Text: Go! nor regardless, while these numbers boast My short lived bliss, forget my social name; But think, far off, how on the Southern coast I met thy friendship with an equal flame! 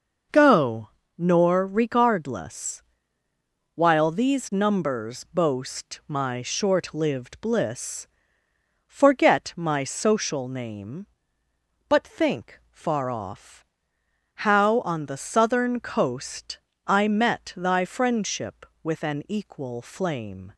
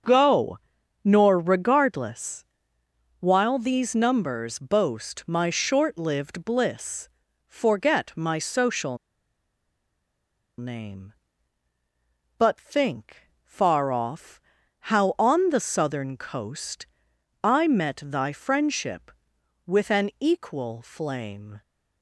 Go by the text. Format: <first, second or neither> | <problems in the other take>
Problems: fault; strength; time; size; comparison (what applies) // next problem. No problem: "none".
first | starts louder than the rest; until 1.5 s; 6.5 dB // pauses between "social" and "name"; strong; at 8.9 s; 1.6 s long // pauses between "coast" and "I"; noticeable; at 16.8 s; 0.58 s long; slight in the first